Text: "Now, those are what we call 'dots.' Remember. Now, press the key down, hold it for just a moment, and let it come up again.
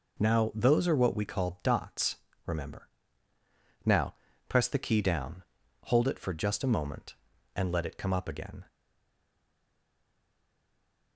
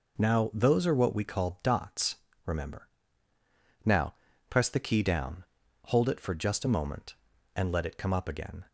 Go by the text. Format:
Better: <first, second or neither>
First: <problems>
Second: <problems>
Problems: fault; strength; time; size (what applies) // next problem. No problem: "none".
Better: second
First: stays silent after the last word; from 8.6 s on; 2.5 s long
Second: none